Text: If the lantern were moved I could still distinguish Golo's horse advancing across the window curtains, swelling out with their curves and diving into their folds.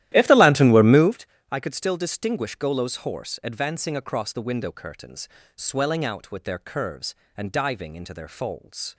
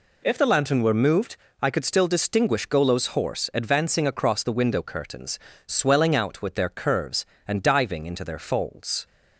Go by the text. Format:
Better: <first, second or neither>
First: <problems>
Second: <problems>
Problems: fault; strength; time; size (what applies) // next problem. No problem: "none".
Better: second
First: starts louder than the rest; strong; until 1.2 s; 13.5 dB // pauses between "moved" and "I"; slight; at 1.2 s; 0.26 s long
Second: pauses between "moved" and "I"; slight; at 1.3 s; 0.26 s long